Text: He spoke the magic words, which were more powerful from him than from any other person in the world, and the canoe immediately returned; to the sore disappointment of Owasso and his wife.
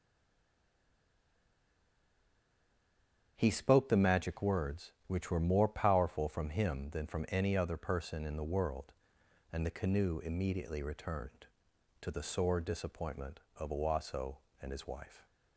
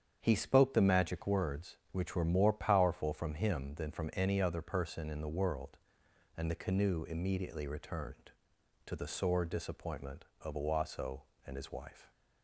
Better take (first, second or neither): second